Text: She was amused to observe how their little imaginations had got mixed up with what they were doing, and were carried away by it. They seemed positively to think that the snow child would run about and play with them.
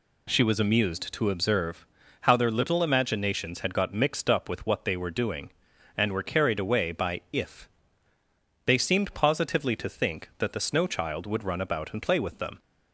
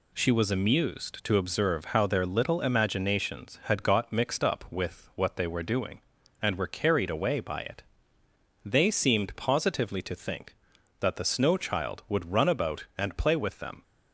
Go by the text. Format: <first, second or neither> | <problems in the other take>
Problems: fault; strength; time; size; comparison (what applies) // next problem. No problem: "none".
second | pauses between "observe" and "how"; slight; at 1.8 s; 0.34 s long // says "if" for "it"; at 7.3 s